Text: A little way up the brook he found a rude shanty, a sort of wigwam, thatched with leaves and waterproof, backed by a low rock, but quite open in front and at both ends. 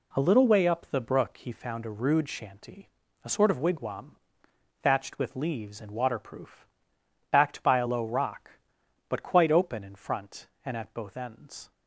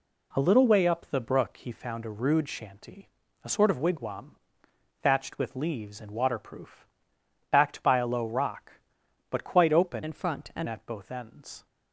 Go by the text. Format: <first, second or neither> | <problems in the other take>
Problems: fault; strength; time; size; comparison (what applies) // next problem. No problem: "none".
first | changes voice from "in" to "and"; from 10.0 to 10.6 s; 0.6 s long